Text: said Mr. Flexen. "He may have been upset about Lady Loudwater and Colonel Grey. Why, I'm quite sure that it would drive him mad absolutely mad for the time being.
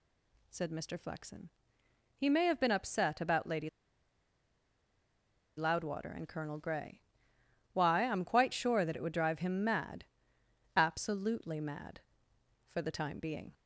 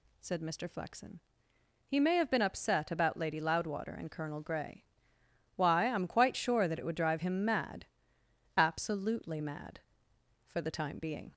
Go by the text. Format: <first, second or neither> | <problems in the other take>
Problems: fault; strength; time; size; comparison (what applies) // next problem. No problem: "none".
second | stays silent before the first word; slight; until 0.5 s; 0.5 s long // pauses between "Lady" and "Loudwater"; strong; at 3.6 s; 1.8 s long // pauses between "mad" and "absolutely"; noticeable; at 10.0 s; 0.72 s long; noticeable in the second